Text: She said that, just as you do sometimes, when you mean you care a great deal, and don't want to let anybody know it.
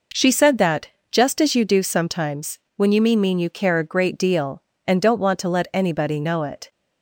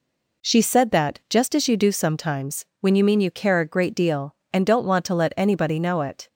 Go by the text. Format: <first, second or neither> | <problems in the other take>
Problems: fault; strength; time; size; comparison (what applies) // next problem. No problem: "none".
second | says "mean" twice; at 3.2 s